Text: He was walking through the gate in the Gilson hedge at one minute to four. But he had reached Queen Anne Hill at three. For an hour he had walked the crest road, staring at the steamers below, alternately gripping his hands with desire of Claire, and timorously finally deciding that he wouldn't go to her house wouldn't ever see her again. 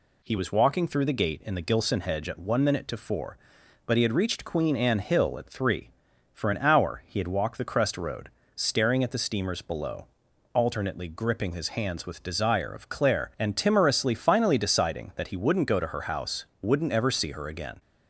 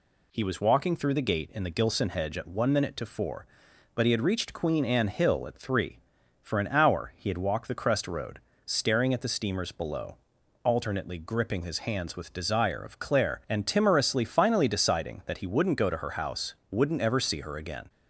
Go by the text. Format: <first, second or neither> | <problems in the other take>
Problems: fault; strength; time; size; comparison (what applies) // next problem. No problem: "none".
neither | pauses between "house" and "wouldn't"; slight; the same in both